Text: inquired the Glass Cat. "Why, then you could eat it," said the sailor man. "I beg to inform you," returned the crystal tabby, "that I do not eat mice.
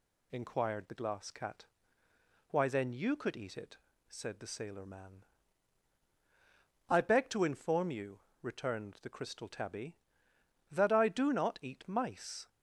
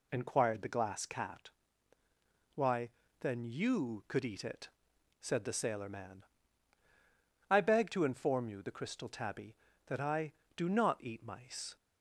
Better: first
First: none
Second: skips "returned"; at 8.6 s

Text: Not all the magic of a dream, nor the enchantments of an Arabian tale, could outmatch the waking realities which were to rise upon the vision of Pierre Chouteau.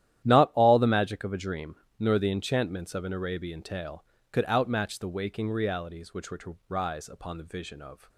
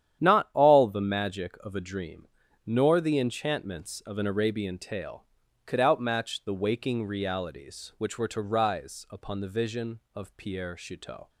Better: second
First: starts louder than the rest; strong; until 1.2 s; 11.5 dB // stops before "Pierre Chouteau"; at 8.0 s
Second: starts louder than the rest; strong; until 1.2 s; 10 dB

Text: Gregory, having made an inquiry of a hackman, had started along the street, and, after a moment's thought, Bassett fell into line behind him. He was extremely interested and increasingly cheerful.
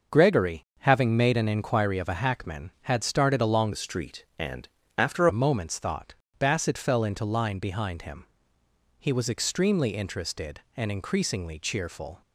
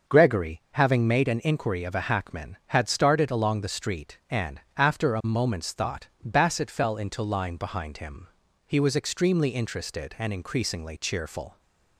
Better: second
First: starts louder than the rest; until 1.2 s; 6 dB // changes voice from "the" to "after"; from 3.7 to 5.2 s; 1.5 s long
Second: starts louder than the rest; until 1.2 s; 6 dB

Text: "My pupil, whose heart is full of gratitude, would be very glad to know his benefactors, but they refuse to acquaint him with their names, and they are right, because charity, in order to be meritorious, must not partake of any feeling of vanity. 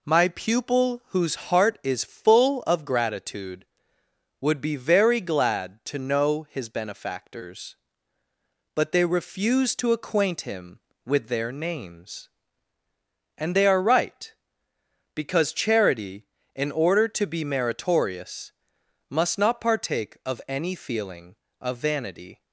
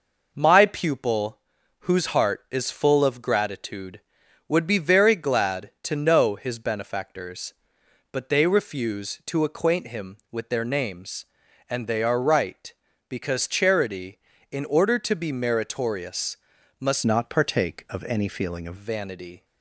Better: first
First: none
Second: changes voice from "not" to "of"; from 17.0 to 18.7 s; 1.7 s long

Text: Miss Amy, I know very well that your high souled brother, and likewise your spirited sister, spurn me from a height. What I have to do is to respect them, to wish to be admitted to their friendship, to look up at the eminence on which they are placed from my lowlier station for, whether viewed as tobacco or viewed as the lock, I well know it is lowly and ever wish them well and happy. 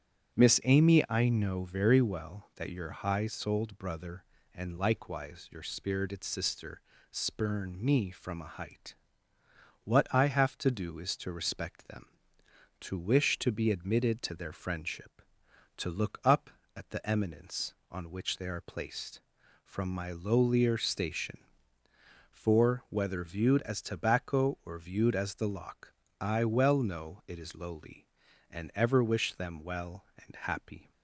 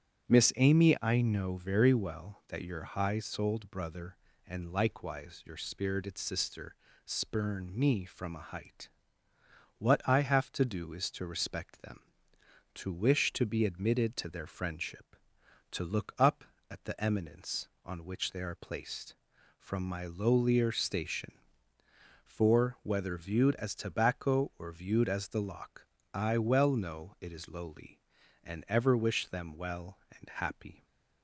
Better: neither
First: starts louder than the rest; strong; until 1.4 s; 7.5 dB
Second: starts louder than the rest; strong; until 1.3 s; 7.5 dB

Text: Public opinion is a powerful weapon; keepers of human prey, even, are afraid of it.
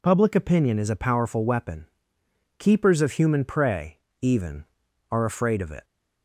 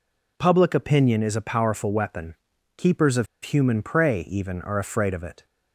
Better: first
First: none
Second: pauses between "of" and "human"; slight; at 3.2 s; 0.18 s long

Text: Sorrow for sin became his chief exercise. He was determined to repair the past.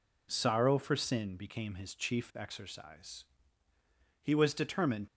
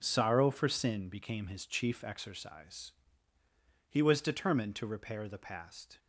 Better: second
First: stops before "to repair the past"; at 5.0 s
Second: none

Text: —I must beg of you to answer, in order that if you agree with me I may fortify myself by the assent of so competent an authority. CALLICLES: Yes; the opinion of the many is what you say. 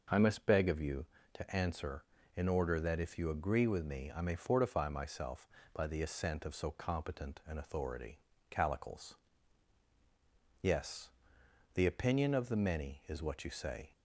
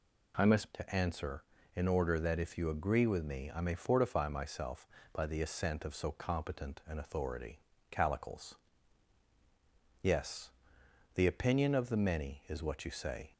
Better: first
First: none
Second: skips "beg of you"; at 0.7 s

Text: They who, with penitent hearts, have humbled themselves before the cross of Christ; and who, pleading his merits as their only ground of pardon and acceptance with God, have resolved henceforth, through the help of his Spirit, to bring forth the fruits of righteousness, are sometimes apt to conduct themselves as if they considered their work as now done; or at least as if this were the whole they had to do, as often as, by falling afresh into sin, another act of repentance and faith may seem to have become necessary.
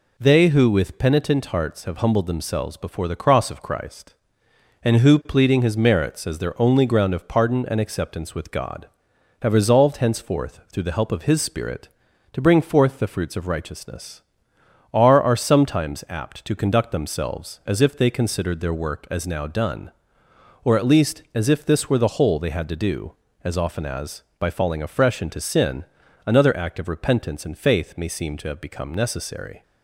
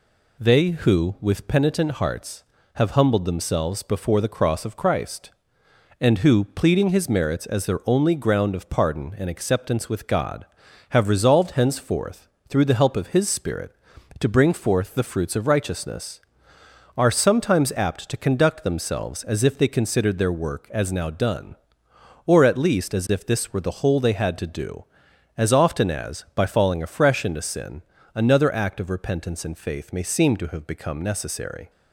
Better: second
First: says "are" twice; at 15.2 s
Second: none

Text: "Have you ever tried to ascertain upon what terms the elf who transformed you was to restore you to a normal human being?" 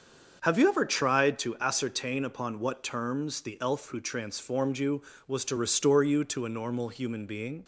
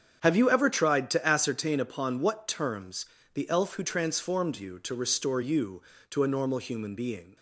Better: first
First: starts louder than the rest; until 1.4 s; 7 dB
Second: starts louder than the rest; strong; until 1.2 s; 8 dB // pauses between "terms" and "the"; slight; at 3.0 s; 0.30 s long // skips "was"; at 4.7 s

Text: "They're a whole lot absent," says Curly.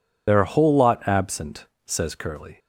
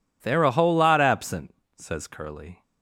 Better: second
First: loses the start of "They're"; at 0.2 s; 55 ms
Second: none

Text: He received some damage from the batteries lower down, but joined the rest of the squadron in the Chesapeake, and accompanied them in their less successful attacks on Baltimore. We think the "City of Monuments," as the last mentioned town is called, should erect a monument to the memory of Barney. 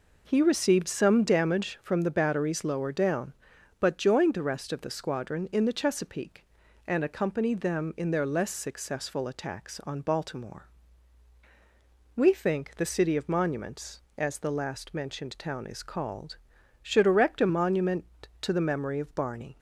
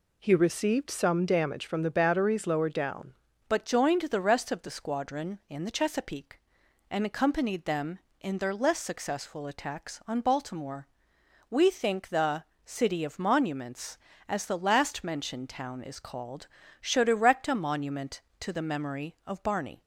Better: first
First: none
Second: changes voice at "but"; from 3.4 s on; 16.4 s long // pauses between "the" and "City"; slight; at 12.4 s; 0.22 s long

